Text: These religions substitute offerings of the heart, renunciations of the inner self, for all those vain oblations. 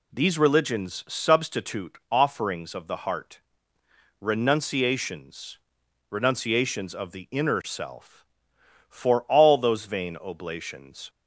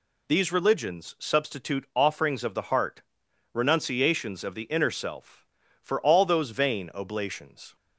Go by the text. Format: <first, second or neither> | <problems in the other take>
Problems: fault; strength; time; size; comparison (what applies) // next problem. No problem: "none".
second | says "renunciations" twice; at 6.0 s